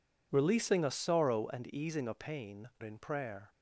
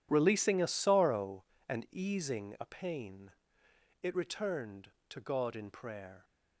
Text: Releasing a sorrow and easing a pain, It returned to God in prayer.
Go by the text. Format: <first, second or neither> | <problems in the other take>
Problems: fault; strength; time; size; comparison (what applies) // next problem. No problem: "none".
second | skips "It returned to God"; at 2.7 s